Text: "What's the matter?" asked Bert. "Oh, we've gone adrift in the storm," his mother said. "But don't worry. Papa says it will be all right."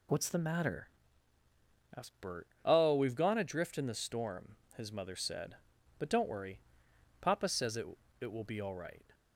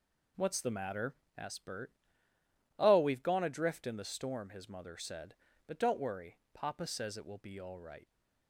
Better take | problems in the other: second | says "it" twice; at 8.1 s

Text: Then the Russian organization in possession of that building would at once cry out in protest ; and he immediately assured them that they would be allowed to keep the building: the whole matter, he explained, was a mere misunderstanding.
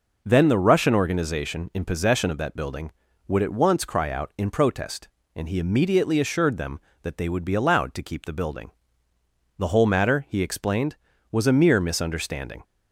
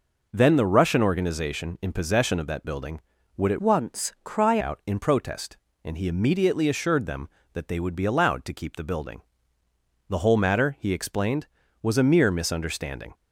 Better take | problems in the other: first | changes voice from "once" to "cry"; from 3.6 to 4.5 s; 0.9 s long

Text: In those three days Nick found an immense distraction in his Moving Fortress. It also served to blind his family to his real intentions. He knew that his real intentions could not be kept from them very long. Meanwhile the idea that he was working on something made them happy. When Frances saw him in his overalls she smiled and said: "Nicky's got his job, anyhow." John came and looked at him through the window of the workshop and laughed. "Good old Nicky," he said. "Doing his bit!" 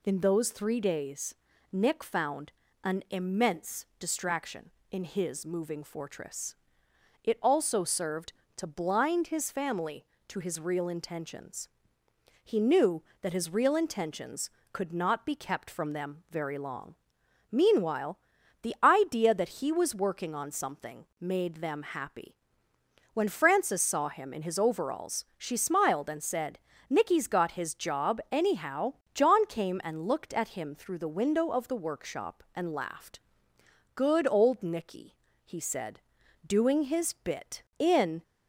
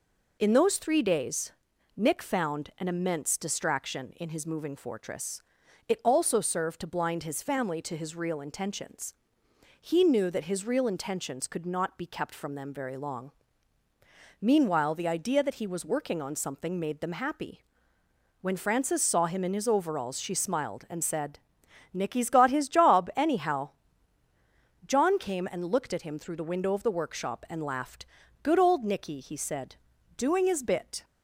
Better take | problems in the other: second | pauses between "days" and "Nick"; at 1.3 s; 0.38 s long; also in the second // pauses between "found" and "an"; slight; at 2.5 s; 0.32 s long // pauses between "Meanwhile" and "the"; at 18.1 s; 0.44 s long // goes on to say "In"; slight; from 37.7 s on; 0.44 s long

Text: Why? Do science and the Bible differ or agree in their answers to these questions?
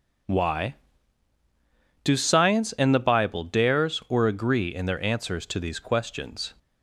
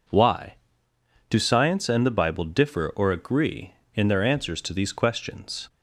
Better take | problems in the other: second | says "dares" for "differ"; at 3.4 s

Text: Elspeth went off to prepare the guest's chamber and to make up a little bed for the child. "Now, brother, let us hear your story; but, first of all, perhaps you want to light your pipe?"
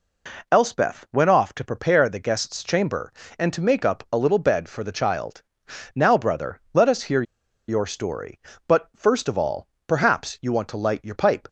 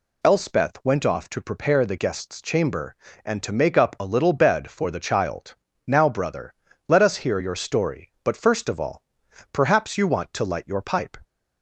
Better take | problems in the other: second | pauses between "hear" and "your"; at 7.2 s; 0.45 s long

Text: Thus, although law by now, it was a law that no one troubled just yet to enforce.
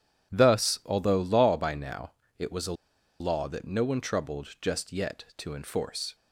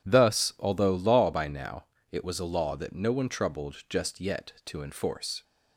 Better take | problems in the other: second | pauses between "a" and "law"; noticeable; at 2.7 s; 0.47 s long

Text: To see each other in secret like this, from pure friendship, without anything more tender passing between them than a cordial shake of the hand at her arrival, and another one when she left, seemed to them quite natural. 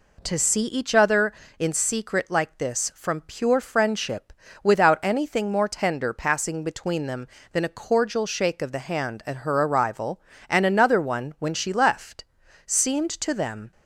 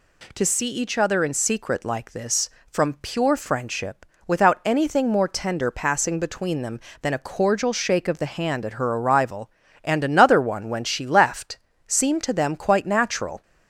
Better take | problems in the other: second | stops before "quite natural"; at 13.7 s

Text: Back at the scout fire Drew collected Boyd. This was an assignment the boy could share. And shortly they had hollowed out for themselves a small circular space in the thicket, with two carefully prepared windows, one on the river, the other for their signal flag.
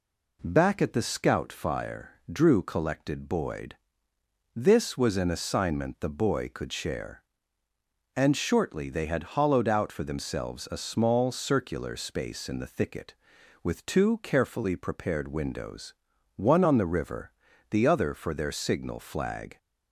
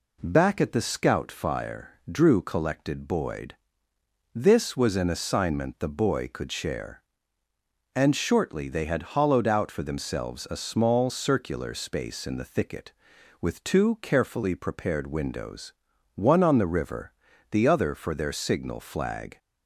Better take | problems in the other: neither | pauses between "fire" and "Drew"; slight; the same in both

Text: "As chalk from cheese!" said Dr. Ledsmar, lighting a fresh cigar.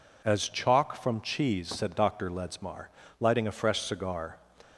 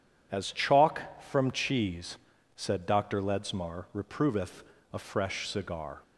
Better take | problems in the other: first | says "reproveth" for "lighting"; at 3.9 s

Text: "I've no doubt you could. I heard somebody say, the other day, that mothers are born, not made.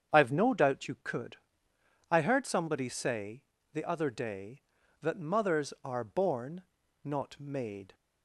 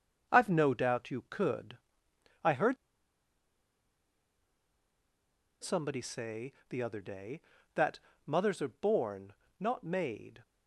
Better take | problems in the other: first | starts louder than the rest; until 1.3 s; 6.5 dB; strong in the first // pauses between "heard" and "somebody"; strong; at 2.7 s; 2.8 s long // pauses between "that" and "mothers"; slight; at 7.9 s; 0.26 s long

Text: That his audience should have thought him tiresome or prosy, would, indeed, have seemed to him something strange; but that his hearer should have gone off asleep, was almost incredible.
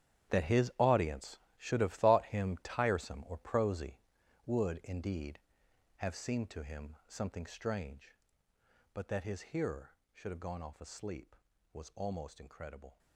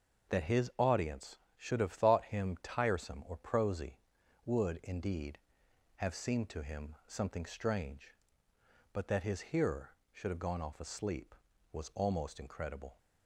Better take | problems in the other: second | gets quieter; strong; throughout; 14.5 dB // starts louder than the rest; strong; until 1.3 s; 10.5 dB; also in the second

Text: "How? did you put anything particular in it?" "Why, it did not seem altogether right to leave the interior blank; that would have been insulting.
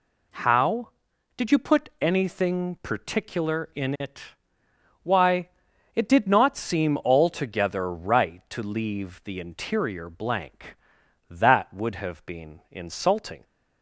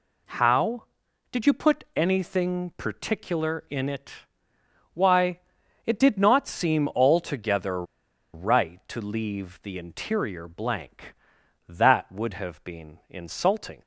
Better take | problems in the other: first | pauses between "altogether" and "right"; noticeable; at 7.8 s; 0.49 s long

